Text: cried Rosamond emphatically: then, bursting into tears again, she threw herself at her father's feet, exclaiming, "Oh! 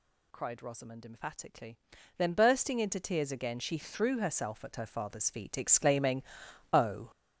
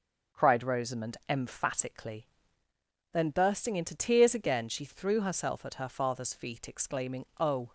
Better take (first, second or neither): second